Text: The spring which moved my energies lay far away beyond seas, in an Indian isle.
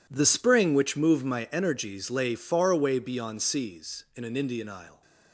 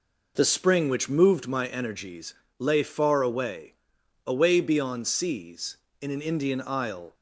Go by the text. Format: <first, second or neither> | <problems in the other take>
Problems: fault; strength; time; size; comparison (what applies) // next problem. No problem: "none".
first | pauses between "energies" and "lay"; slight; at 2.3 s; 0.24 s long // says "away" twice; at 4.2 s